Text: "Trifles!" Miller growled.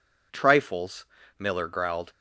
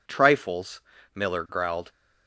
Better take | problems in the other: neither | none

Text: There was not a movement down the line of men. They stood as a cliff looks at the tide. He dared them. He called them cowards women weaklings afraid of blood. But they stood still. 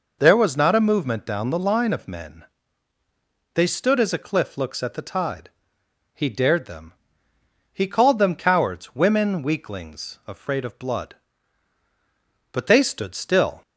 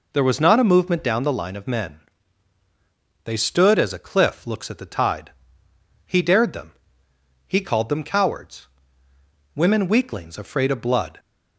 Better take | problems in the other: first | pauses between "cowards" and "women"; noticeable; at 8.6 s; 0.88 s long // stops before "But they stood still"; at 11.1 s

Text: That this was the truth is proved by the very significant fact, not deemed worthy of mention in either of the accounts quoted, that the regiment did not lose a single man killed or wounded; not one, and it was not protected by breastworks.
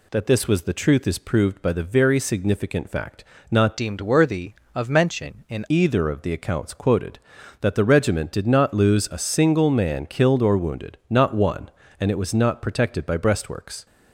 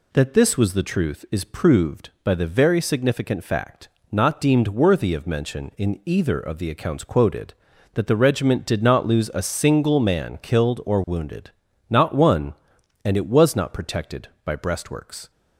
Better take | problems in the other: second | changes voice from "deemed" to "in"; from 3.7 to 5.6 s; 1.9 s long

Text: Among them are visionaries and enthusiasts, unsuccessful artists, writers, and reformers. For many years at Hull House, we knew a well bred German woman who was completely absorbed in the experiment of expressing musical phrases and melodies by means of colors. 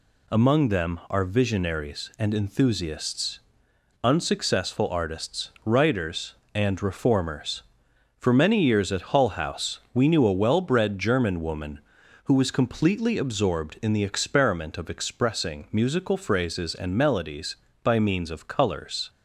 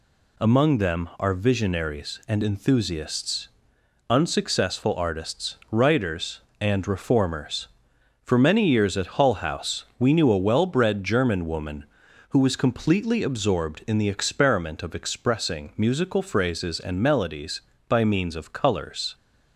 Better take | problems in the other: neither | none

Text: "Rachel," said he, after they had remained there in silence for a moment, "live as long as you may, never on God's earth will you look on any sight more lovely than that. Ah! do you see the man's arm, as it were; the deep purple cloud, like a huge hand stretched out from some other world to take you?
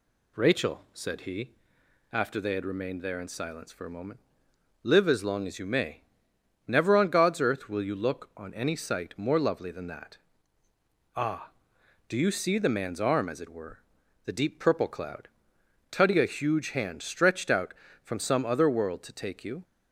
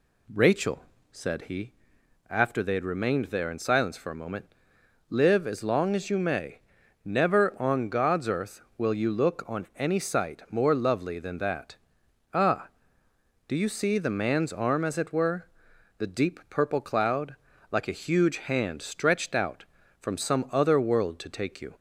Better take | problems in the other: second | says "tutty" for "like"; at 15.9 s

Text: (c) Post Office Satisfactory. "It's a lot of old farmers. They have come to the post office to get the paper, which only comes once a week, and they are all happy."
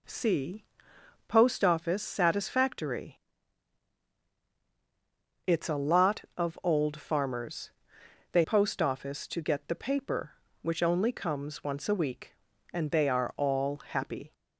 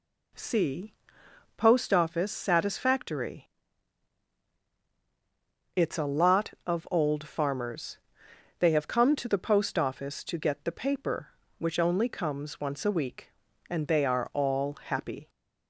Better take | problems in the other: second | skips "have come to the"; at 8.4 s

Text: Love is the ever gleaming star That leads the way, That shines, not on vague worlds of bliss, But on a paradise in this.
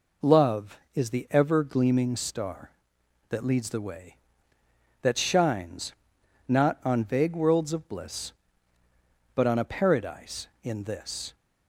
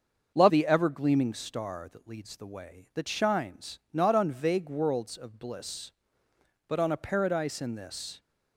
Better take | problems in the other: first | starts louder than the rest; until 1.3 s; 6.5 dB // skips "is"; at 0.4 s

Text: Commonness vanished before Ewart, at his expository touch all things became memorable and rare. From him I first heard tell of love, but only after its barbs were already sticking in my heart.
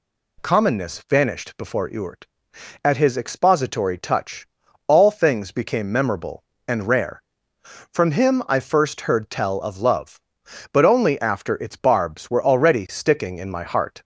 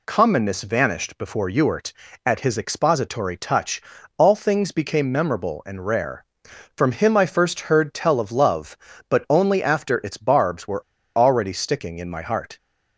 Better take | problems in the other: first | pauses between "touch" and "all"; slight; at 3.8 s; 0.34 s long; also in the first // pauses between "were" and "already"; slight; at 10.8 s; 0.32 s long

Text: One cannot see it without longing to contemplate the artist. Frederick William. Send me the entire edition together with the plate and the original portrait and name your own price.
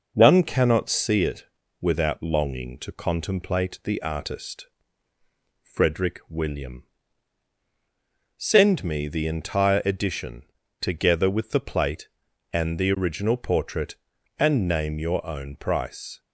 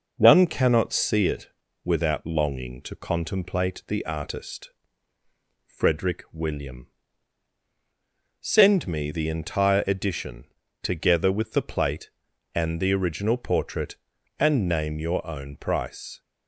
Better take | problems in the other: neither | pauses between "it" and "without"; slight; the same in both // pauses between "edition" and "together"; the same in both

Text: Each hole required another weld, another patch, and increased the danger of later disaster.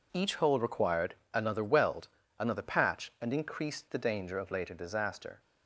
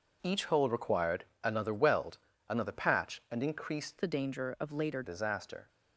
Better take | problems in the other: first | pauses between "required" and "another"; slight; at 1.2 s; 0.20 s long; slight in the first // changes voice from "the" to "later"; from 4.0 to 5.0 s; 1.0 s long

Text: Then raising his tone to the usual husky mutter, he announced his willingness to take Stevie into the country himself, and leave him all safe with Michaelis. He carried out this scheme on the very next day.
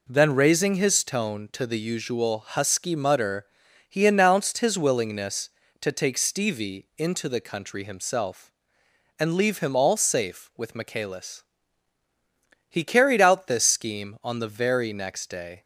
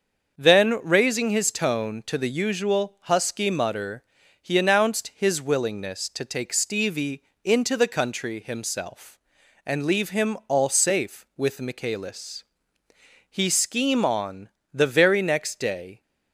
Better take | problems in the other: first | starts louder than the rest; until 1.4 s; 6.5 dB // pauses between "Stevie" and "into"; slight; at 7.2 s; 0.22 s long // skips "carried out this"; at 13.4 s // pauses between "on" and "the"; slight; at 14.4 s; 0.24 s long

